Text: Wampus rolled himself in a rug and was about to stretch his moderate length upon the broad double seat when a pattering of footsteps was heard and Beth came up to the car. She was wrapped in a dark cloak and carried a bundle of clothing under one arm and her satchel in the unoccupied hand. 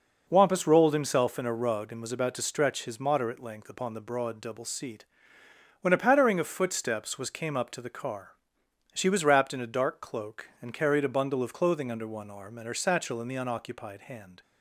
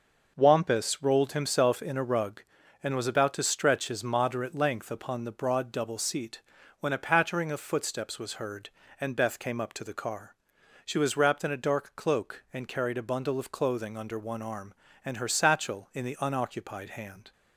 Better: second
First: pauses between "seat" and "when"; noticeable; at 5.0 s; 0.76 s long // skips "heard and Beth"; at 7.2 s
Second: pauses between "seat" and "when"; at 6.3 s; 0.40 s long

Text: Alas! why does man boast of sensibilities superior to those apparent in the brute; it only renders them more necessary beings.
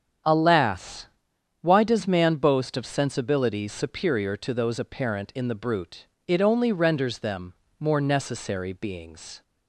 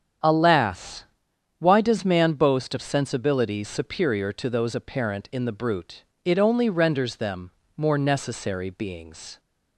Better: neither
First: starts louder than the rest; strong; until 1.7 s; 8 dB // pauses between "them" and "more"; slight; at 7.5 s; 0.26 s long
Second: starts louder than the rest; strong; until 1.7 s; 8 dB // pauses between "them" and "more"; slight; at 7.5 s; 0.26 s long

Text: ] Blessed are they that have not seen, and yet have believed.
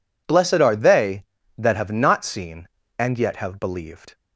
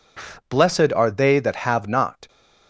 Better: first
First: none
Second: stops before "seen and yet have believed"; at 2.2 s

